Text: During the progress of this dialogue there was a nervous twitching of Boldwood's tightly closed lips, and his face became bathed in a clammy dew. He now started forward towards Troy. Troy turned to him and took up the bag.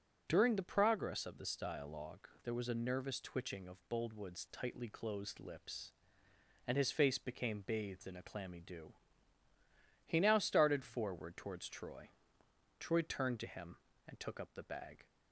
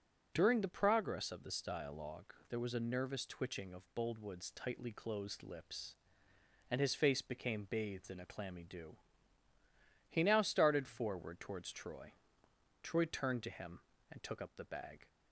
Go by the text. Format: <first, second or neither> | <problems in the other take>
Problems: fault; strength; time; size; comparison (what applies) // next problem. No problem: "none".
neither | pauses between "dialogue" and "there"; slight; the same in both